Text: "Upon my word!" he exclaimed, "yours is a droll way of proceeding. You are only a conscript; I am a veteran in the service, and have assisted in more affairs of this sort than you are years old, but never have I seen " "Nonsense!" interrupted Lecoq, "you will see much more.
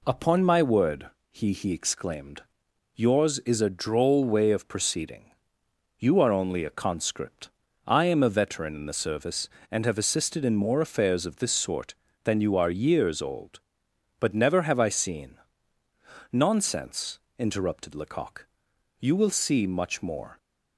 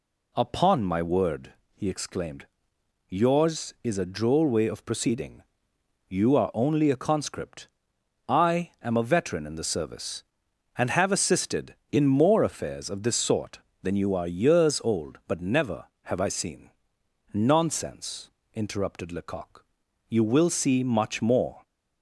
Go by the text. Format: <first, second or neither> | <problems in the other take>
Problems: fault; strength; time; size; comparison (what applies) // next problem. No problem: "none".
second | says "he" twice; at 1.5 s